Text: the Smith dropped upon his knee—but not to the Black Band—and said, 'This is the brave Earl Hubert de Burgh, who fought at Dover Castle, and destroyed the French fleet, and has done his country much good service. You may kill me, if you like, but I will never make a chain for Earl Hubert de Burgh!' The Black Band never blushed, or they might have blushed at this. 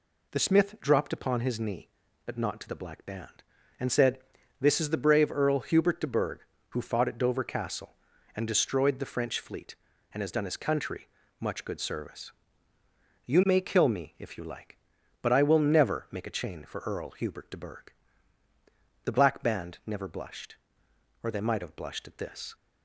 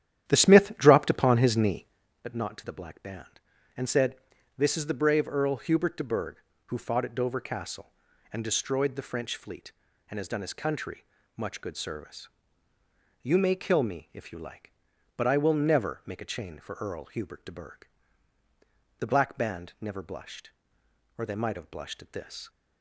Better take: first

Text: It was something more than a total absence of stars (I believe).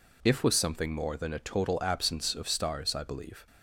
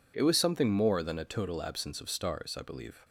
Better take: second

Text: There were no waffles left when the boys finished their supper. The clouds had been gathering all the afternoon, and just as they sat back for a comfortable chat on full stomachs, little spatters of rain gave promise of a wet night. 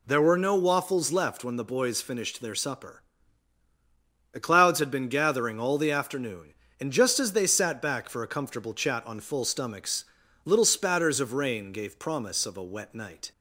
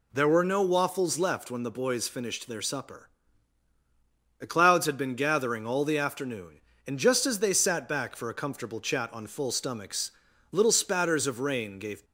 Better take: first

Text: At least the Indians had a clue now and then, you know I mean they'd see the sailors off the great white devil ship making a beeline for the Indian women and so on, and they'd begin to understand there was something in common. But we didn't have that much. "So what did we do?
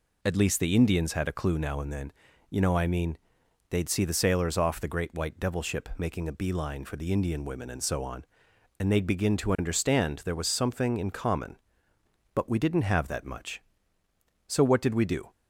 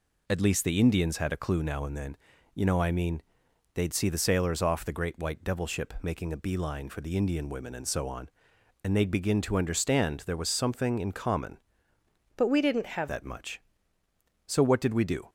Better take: first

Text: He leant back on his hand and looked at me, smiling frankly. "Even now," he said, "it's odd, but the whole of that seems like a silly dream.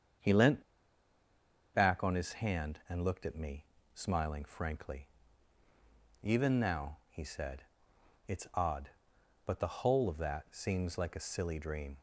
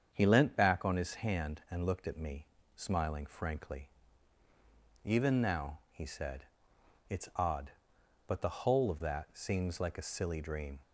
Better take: second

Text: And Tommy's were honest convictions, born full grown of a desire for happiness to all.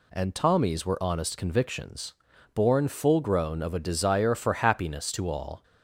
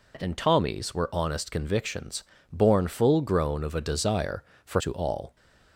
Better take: first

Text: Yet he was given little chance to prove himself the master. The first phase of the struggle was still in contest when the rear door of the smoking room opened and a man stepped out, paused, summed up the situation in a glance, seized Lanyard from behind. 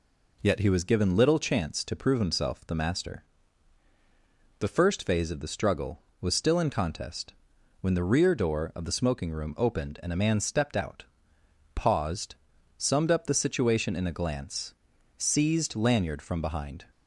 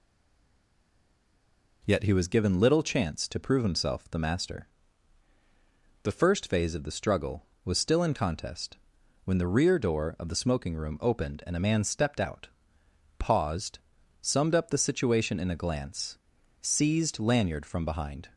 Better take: first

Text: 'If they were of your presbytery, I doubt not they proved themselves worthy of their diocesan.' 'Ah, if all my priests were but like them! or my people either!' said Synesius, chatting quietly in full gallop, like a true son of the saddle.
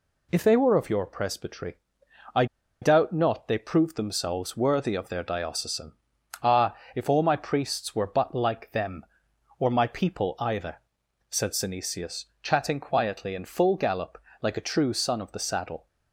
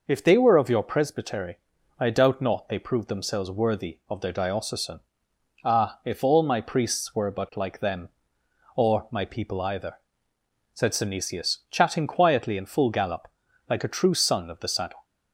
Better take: second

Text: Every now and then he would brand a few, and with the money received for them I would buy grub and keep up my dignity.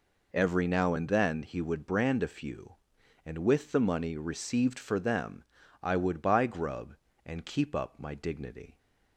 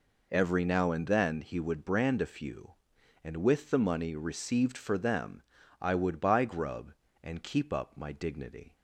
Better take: neither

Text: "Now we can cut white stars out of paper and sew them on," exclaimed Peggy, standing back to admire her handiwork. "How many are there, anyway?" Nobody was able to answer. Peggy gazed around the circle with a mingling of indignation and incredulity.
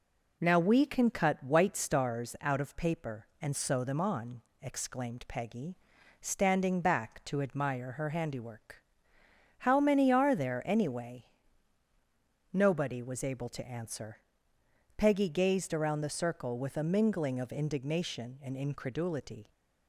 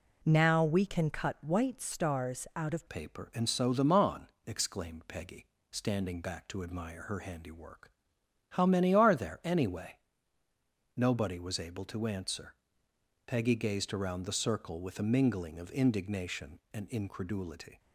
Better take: first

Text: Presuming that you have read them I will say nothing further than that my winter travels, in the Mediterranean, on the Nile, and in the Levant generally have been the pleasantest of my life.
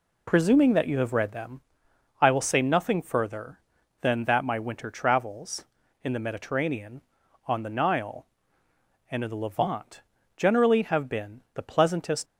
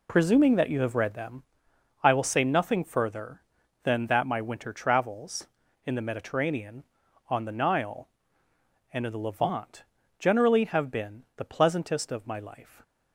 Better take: second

